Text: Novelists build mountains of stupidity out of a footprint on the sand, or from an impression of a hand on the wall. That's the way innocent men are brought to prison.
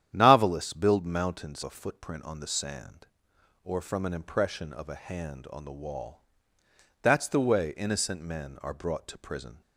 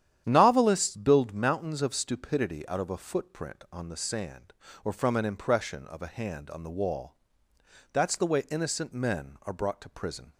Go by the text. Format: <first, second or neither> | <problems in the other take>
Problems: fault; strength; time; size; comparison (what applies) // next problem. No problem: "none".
second | starts louder than the rest; strong; until 1.1 s; 10 dB; strong in the second // skips "of stupidity out of"; at 1.6 s